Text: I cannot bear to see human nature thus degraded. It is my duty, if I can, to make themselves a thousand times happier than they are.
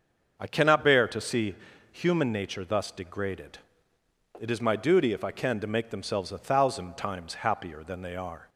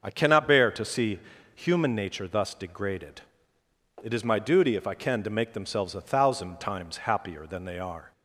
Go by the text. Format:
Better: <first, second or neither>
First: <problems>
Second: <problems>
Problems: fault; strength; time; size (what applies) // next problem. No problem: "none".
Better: neither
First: starts louder than the rest; until 1.4 s; 6.5 dB // pauses between "see" and "human"; slight; at 1.5 s; 0.36 s long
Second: starts louder than the rest; until 1.0 s; 6.5 dB // pauses between "see" and "human"; slight; at 1.1 s; 0.35 s long